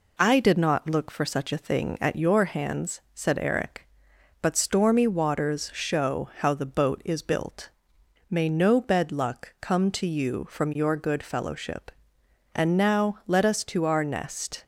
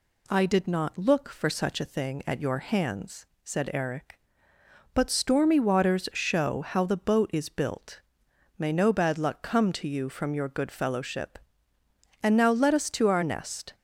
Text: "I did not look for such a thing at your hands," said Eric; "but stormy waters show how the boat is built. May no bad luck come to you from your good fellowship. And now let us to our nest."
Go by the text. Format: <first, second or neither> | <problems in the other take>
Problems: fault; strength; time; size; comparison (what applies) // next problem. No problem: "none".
second | says "bed" for "bad"; at 8.7 s